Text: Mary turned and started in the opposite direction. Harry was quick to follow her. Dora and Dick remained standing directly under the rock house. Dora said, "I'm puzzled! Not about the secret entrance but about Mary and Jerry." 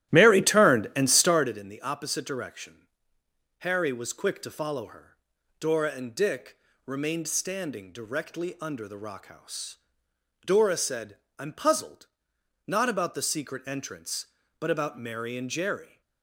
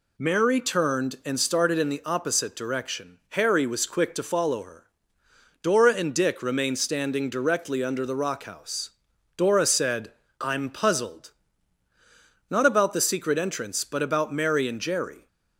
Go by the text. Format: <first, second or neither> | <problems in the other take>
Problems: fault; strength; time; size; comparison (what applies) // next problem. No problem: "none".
second | starts louder than the rest; strong; until 1.5 s; 14 dB // pauses between "Dick" and "remained"; slight; at 6.5 s; 0.30 s long